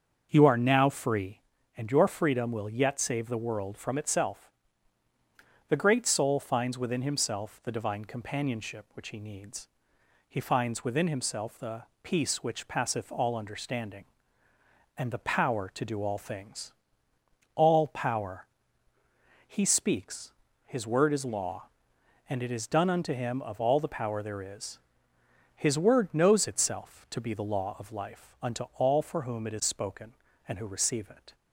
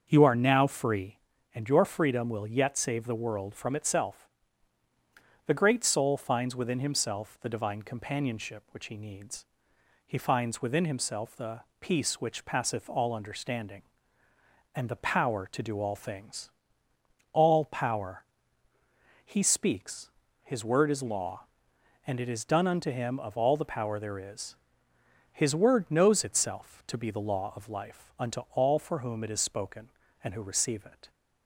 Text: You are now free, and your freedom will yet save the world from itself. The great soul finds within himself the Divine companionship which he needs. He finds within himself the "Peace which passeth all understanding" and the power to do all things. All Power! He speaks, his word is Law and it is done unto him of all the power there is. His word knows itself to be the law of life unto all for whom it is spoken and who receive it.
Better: neither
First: starts louder than the rest; until 1.3 s; 7 dB // pauses between "the" and "Peace"; slight; at 11.8 s; 0.18 s long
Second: starts louder than the rest; until 1.1 s; 6.5 dB // pauses between "the" and "Peace"; slight; at 11.6 s; 0.18 s long

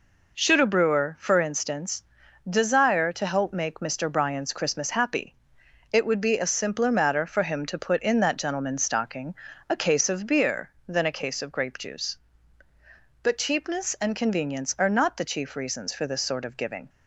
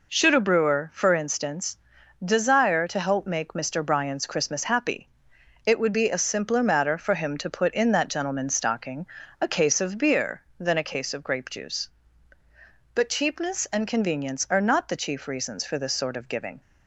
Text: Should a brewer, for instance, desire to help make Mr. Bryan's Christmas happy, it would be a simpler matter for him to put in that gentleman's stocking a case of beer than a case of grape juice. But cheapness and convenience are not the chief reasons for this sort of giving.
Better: neither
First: pauses between "stocking" and "a"; slight; at 9.3 s; 0.36 s long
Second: pauses between "stocking" and "a"; slight; at 9.0 s; 0.36 s long

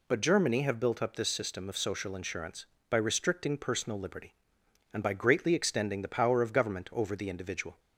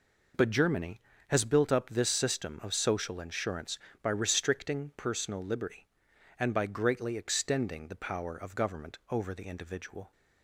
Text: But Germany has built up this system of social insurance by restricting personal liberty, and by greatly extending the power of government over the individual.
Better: second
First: says "have" for "has"; at 0.6 s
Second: none

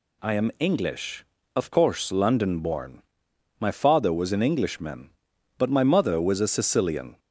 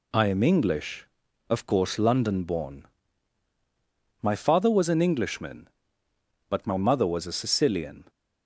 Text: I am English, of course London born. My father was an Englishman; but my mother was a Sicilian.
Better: neither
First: none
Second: none

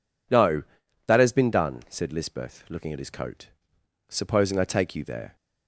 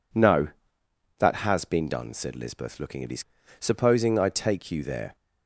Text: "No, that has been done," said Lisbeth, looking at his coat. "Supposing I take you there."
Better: first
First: none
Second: skips "coat"; at 3.4 s

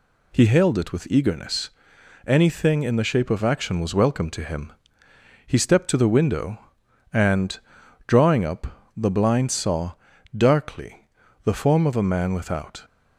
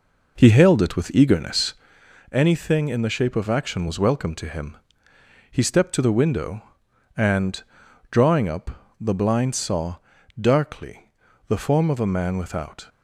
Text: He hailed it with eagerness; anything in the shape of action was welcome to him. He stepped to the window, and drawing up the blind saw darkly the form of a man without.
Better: first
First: pauses between "and" and "drawing"; noticeable; at 7.5 s; 0.48 s long // pauses between "saw" and "darkly"; at 9.9 s; 0.38 s long // pauses between "darkly" and "the"; slight; at 11.0 s; 0.34 s long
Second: starts louder than the rest; noticeable; until 2.0 s; 5 dB // pauses between "and" and "drawing"; noticeable; at 7.6 s; 0.48 s long // pauses between "saw" and "darkly"; at 9.9 s; 0.38 s long // pauses between "darkly" and "the"; slight; at 11.1 s; 0.34 s long

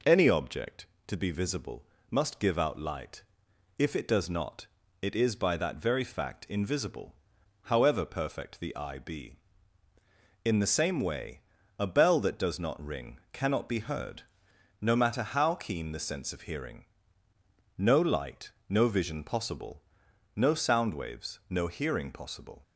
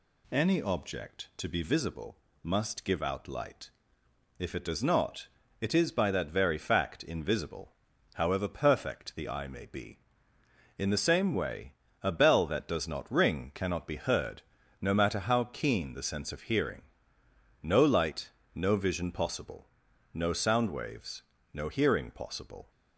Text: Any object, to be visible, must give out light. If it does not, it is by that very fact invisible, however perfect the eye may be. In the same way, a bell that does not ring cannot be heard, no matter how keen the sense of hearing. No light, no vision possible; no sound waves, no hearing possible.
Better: second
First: skips "may"; at 8.9 s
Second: none

